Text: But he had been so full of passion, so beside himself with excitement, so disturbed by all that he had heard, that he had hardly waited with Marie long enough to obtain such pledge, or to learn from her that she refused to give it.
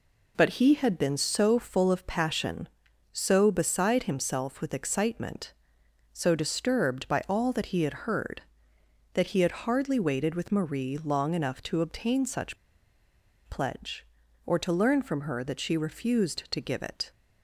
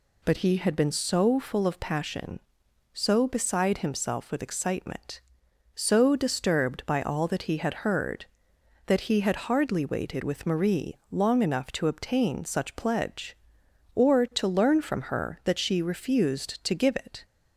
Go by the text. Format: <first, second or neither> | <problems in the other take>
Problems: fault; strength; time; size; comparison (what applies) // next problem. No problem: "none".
second | pauses between "such" and "pledge"; noticeable; at 12.5 s; 0.91 s long